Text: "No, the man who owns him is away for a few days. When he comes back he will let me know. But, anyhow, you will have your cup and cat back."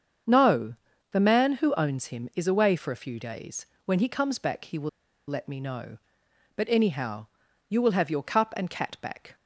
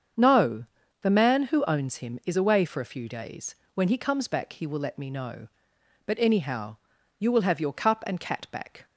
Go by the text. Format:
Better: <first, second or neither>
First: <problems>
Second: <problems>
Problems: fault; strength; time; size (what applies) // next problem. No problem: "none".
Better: second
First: starts louder than the rest; strong; until 1.6 s; 7 dB // pauses between "will" and "let"; at 4.8 s; 0.39 s long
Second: starts louder than the rest; strong; until 1.5 s; 7 dB